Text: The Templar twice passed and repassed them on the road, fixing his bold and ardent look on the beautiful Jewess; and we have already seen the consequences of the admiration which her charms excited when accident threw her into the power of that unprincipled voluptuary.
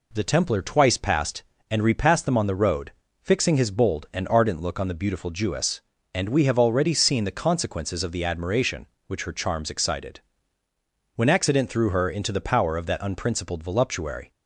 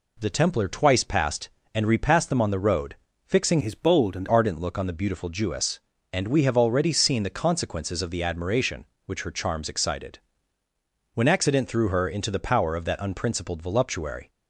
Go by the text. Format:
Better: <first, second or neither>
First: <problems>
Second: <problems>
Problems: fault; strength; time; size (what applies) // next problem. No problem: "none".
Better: first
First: pauses between "excited" and "when"; noticeable; at 10.2 s; 0.96 s long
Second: changes voice from "his" to "and"; from 3.6 to 4.2 s; 0.6 s long // pauses between "excited" and "when"; noticeable; at 10.1 s; 0.96 s long